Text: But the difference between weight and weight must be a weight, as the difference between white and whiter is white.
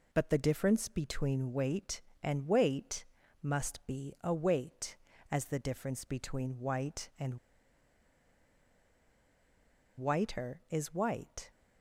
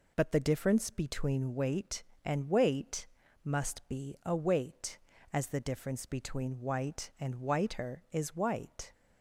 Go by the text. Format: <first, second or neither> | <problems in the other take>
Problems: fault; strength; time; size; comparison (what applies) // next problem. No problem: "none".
second | pauses between "weight" and "must"; slight; at 3.0 s; 0.36 s long; slight in the second // pauses between "and" and "whiter"; strong; at 7.3 s; 2.6 s long